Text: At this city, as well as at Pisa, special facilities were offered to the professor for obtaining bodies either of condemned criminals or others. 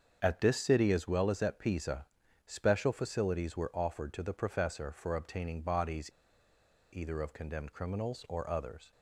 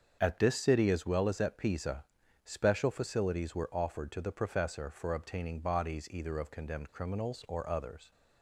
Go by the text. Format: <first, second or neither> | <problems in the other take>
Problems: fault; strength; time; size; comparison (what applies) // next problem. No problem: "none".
second | starts louder than the rest; until 1.2 s; 7 dB; also in the second // pauses between "bodies" and "either"; noticeable; at 6.0 s; 0.84 s long